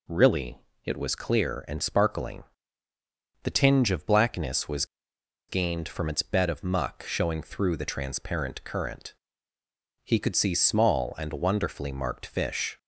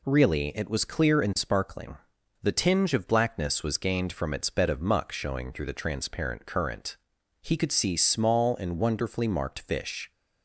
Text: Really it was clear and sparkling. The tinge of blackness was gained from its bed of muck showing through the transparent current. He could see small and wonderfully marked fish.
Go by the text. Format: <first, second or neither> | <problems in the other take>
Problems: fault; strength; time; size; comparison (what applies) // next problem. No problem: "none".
second | pauses between "Really" and "it"; slight; at 0.5 s; 0.26 s long // pauses between "was" and "gained"; noticeable; at 4.8 s; 0.64 s long